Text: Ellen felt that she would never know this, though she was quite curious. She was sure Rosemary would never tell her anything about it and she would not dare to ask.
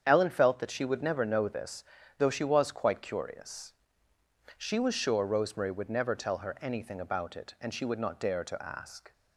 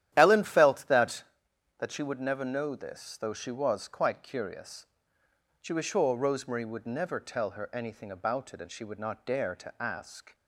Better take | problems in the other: first | starts louder than the rest; strong; until 1.1 s; 11.5 dB; strong in the first // says "that" twice; at 1.7 s

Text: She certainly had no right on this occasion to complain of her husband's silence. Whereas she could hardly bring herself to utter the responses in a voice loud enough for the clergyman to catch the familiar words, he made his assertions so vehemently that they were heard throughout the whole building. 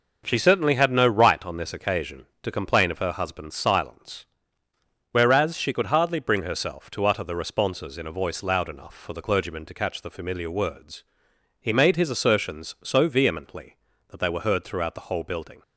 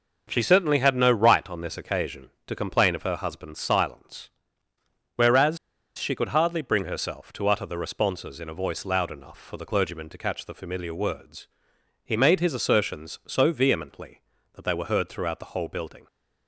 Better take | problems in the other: first | pauses between "Whereas" and "she"; at 5.5 s; 0.38 s long

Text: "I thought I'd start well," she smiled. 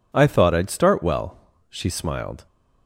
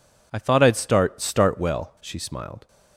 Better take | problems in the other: first | says "start" twice; at 1.2 s

